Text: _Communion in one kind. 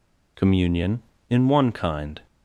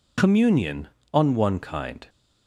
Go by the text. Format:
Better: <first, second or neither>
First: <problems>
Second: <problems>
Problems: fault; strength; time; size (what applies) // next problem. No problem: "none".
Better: first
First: none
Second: says "on" for "in"; at 1.1 s